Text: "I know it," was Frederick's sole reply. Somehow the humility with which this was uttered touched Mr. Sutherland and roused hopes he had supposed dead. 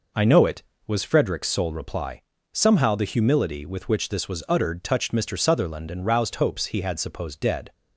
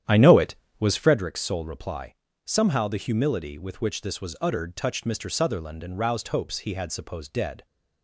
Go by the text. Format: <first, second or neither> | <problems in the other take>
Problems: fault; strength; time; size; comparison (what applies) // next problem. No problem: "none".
first | starts louder than the rest; strong; until 1.3 s; 10 dB